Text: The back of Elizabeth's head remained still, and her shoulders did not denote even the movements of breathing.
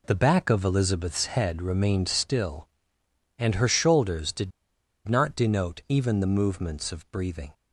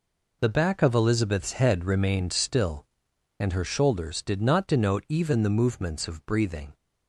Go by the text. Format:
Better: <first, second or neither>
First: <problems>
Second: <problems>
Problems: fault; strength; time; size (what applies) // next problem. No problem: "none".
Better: second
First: pauses between "did" and "not"; noticeable; at 4.5 s; 0.56 s long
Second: none